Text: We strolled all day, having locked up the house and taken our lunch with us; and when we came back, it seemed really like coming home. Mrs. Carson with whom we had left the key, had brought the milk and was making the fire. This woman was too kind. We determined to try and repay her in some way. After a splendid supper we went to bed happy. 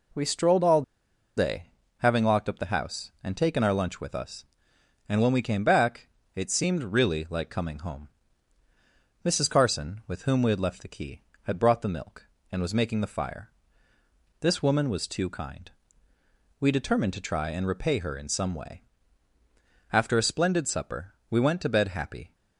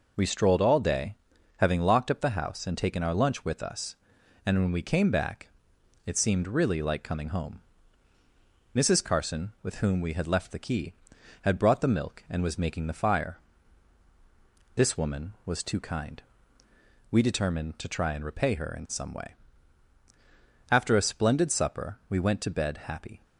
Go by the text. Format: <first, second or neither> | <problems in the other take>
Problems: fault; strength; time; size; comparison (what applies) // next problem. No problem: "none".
second | pauses between "all" and "day"; noticeable; at 0.8 s; 0.54 s long // pauses between "supper" and "we"; slight; at 21.1 s; 0.16 s long